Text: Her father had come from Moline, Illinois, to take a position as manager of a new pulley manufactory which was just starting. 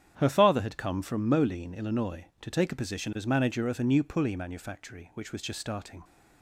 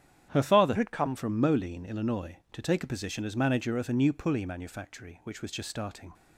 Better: first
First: starts louder than the rest; strong; until 1.1 s; 9.5 dB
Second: starts louder than the rest; strong; until 1.3 s; 10 dB // changes voice from "had" to "come"; from 0.7 to 1.1 s; 0.4 s long

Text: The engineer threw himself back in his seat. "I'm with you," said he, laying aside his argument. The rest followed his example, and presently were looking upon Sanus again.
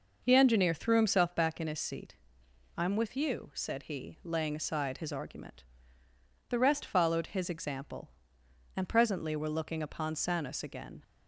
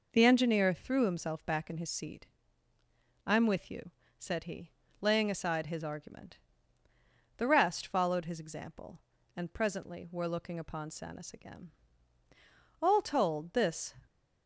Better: first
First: none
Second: goes on to say "All told this"; noticeable; from 12.8 s on; 1.1 s long

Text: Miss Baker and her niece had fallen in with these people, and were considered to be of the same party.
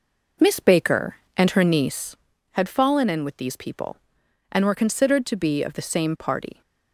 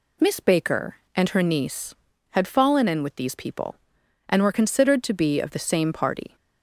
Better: second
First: starts louder than the rest; noticeable; until 2.2 s; 4.5 dB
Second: none

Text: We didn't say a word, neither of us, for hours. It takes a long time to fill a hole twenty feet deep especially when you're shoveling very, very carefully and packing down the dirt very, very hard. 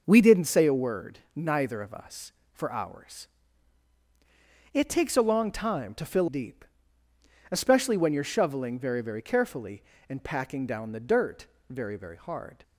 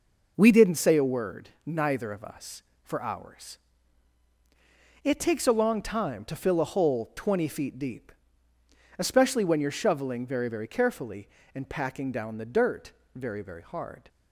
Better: second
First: skips "a hole twenty feet"; at 6.2 s // pauses between "deep" and "especially"; noticeable; at 6.6 s; 0.86 s long // pauses between "dirt" and "very"; slight; at 11.4 s; 0.24 s long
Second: pauses between "deep" and "especially"; noticeable; at 8.1 s; 0.86 s long // pauses between "dirt" and "very"; slight; at 12.9 s; 0.24 s long

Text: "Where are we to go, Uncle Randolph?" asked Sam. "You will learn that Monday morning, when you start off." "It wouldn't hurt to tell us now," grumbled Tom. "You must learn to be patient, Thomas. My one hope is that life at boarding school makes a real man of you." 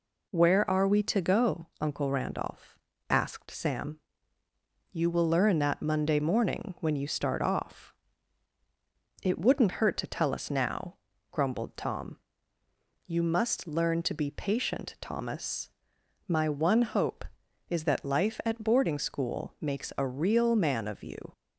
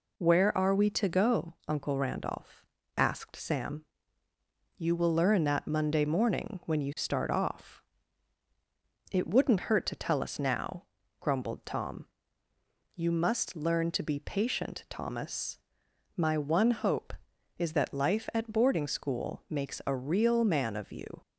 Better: neither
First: none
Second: none

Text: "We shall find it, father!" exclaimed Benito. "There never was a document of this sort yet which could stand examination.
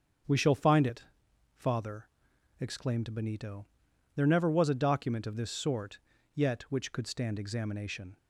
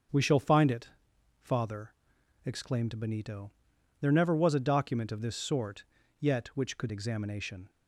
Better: first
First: starts louder than the rest; until 1.8 s; 7 dB // pauses between "sort" and "yet"; slight; at 5.9 s; 0.34 s long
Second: starts louder than the rest; until 1.6 s; 7 dB // pauses between "sort" and "yet"; slight; at 5.8 s; 0.34 s long // skips "stand"; at 6.9 s

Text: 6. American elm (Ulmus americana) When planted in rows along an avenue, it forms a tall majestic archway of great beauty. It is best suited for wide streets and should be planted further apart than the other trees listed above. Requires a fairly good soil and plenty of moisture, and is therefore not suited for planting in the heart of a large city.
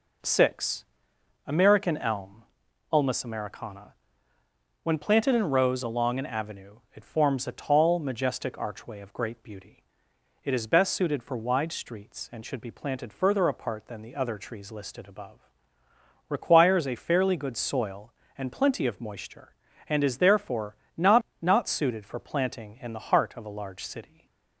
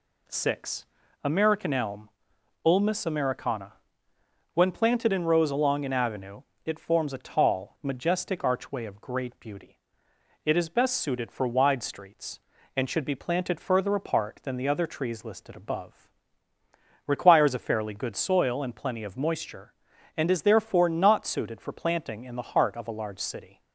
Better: second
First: pauses between "therefore" and "not"; slight; at 20.7 s; 0.22 s long // says "not" twice; at 21.3 s // stays silent after the last word; slight; from 24.0 s on; 0.6 s long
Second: none

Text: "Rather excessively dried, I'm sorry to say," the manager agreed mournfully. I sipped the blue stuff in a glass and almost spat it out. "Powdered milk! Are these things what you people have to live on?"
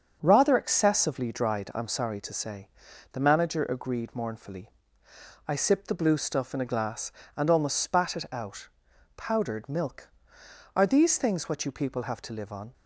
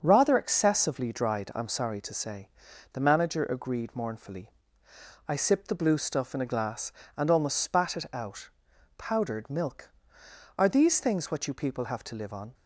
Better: neither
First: starts louder than the rest; until 1.2 s; 6.5 dB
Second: starts louder than the rest; strong; until 1.0 s; 7 dB

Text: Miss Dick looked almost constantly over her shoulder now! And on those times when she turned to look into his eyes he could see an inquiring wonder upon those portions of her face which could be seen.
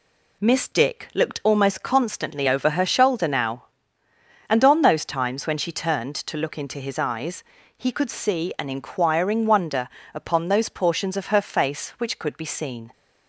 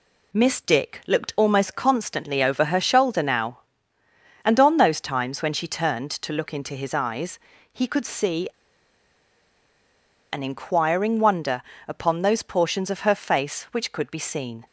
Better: first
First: pauses between "eyes" and "he"; slight; at 7.4 s; 0.36 s long // pauses between "wonder" and "upon"; slight; at 9.8 s; 0.26 s long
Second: pauses between "eyes" and "he"; slight; at 7.3 s; 0.36 s long // pauses between "see" and "an"; strong; at 8.4 s; 1.8 s long // pauses between "wonder" and "upon"; slight; at 11.6 s; 0.26 s long

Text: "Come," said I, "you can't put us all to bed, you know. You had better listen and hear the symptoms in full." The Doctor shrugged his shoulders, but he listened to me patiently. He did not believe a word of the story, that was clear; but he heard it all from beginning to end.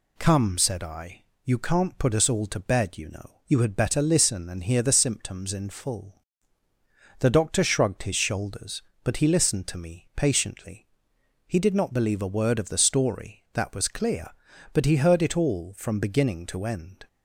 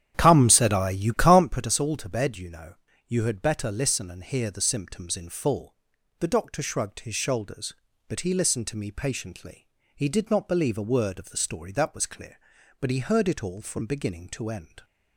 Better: first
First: none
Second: starts louder than the rest; strong; until 1.7 s; 10 dB

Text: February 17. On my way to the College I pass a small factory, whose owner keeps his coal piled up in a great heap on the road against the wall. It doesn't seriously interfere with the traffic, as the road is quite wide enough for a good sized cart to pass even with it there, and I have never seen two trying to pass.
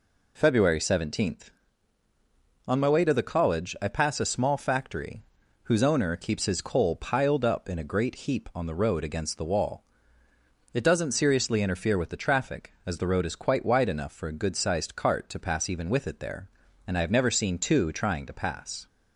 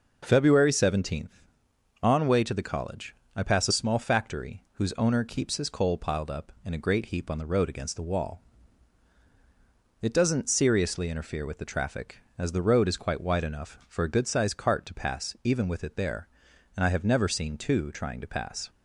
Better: first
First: none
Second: skips "my"; at 2.2 s // pauses between "College" and "I"; slight; at 3.1 s; 0.22 s long

